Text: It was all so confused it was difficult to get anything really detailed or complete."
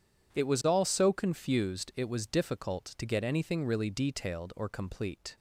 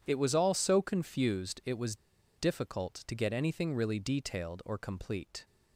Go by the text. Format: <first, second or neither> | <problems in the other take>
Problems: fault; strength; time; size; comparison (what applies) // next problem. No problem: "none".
first | pauses between "was" and "difficult"; at 1.9 s; 0.42 s long